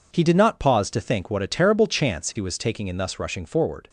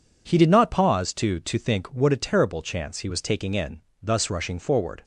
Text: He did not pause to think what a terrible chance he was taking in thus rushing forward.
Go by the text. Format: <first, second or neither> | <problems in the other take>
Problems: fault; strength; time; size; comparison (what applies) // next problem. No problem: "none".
first | says "to" twice; at 1.3 s // pauses between "in" and "thus"; slight; at 3.8 s; 0.18 s long